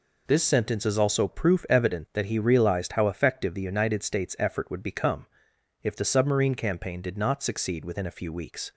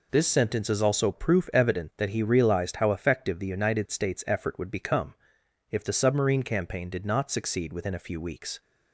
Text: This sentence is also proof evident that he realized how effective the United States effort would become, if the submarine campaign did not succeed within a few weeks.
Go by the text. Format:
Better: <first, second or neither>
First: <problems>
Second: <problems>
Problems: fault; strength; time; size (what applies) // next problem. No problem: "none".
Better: neither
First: none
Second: none